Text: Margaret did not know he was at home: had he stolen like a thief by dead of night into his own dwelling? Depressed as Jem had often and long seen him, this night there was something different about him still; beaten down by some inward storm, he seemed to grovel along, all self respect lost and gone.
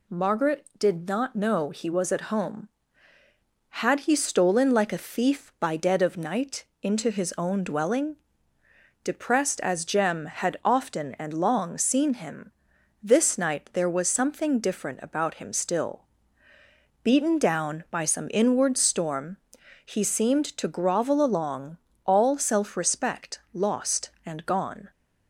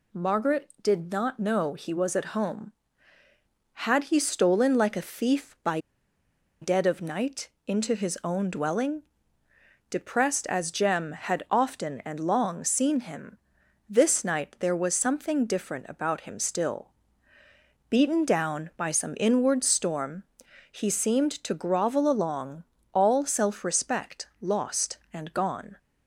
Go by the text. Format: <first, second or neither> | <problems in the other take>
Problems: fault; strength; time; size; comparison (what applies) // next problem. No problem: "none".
first | pauses between "by" and "dead"; noticeable; at 5.7 s; 0.82 s long // pauses between "night" and "into"; slight; at 7.4 s; 0.18 s long; slight in the first